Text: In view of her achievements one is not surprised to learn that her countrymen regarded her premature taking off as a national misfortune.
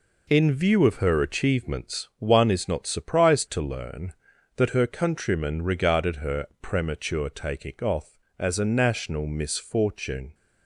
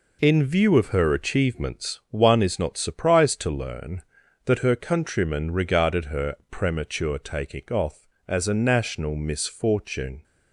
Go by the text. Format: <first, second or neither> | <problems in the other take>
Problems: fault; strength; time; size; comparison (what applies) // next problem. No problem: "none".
neither | pauses between "her" and "premature"; slight; the same in both